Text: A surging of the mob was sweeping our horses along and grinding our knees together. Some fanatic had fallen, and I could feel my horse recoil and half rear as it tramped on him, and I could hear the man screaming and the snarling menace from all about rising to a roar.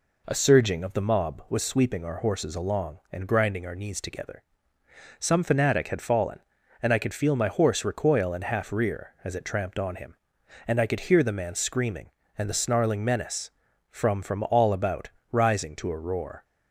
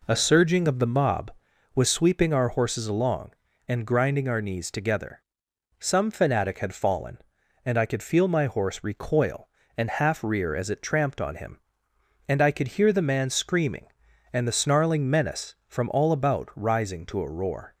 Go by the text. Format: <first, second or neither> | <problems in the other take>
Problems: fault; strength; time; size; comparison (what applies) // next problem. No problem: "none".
second | says "from" twice; at 14.2 s // pauses between "about" and "rising"; slight; at 15.0 s; 0.20 s long